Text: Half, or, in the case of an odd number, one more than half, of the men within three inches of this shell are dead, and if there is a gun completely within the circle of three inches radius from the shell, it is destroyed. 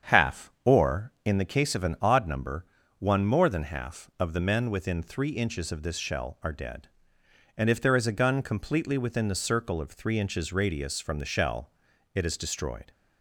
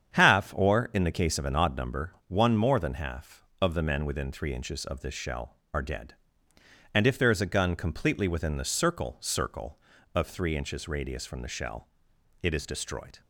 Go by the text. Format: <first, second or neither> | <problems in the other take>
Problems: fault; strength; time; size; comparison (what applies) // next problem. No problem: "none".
first | starts louder than the rest; strong; until 1.1 s; 8 dB; strong in the first // says "circle" twice; at 9.2 s